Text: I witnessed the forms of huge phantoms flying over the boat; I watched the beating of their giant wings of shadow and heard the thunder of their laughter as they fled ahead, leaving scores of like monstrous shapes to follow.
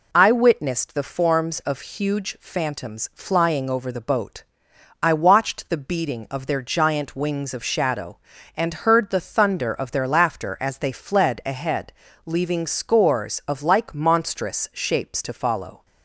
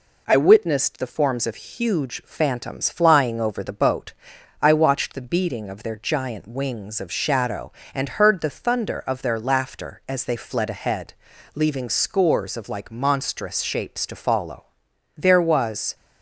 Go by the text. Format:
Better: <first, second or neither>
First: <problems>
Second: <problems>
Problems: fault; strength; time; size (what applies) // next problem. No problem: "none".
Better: first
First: none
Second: goes on to say "There was"; noticeable; from 15.1 s on; 0.80 s long